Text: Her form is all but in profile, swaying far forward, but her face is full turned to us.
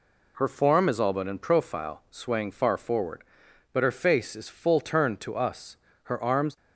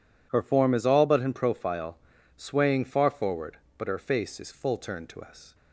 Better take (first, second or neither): second